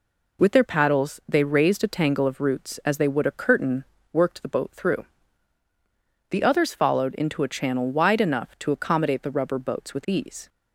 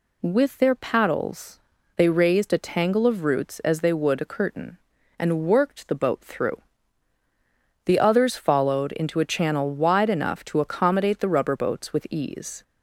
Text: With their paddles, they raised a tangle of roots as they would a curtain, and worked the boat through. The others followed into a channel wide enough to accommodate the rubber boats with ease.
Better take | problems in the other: second | skips "and"; at 3.9 s

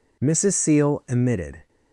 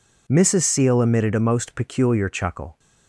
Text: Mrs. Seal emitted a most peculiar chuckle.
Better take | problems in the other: second | stops before "a most peculiar chuckle"; at 1.6 s

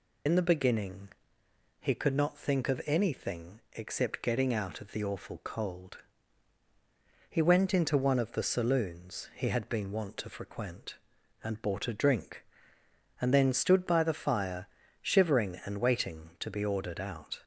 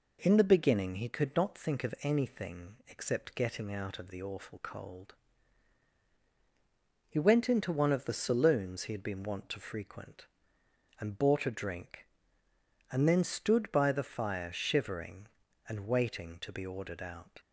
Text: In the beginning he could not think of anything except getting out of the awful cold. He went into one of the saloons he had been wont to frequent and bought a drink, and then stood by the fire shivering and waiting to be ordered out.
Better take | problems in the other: second | loses the start of "In"; at 0.2 s; 85 ms // pauses between "beginning" and "he"; noticeable; at 1.0 s; 0.72 s long // pauses between "fire" and "shivering"; slight; at 14.6 s; 0.34 s long

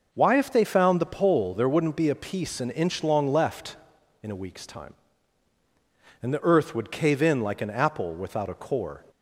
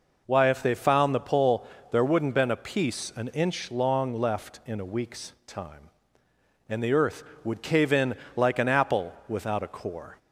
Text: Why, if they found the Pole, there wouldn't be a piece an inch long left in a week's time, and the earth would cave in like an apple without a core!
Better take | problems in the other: first | says "been" for "be"; at 2.3 s // pauses between "in" and "like"; slight; at 8.1 s; 0.20 s long

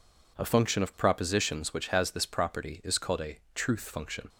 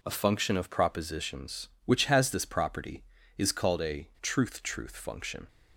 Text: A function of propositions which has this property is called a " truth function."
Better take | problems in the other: first | says "truth" twice; at 4.6 s

